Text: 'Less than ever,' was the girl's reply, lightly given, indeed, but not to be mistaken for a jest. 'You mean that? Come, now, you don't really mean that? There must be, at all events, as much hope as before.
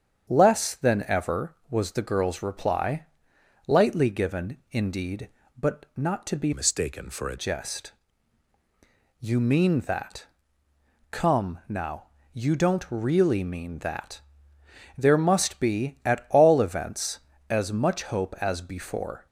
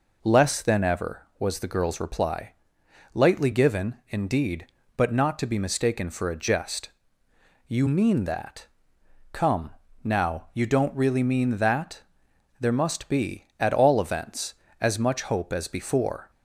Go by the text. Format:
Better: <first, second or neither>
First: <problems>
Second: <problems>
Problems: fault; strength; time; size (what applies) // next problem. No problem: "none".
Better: second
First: starts louder than the rest; strong; until 1.3 s; 8 dB // changes voice from "mistaken" to "a"; from 6.5 to 7.3 s; 0.8 s long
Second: none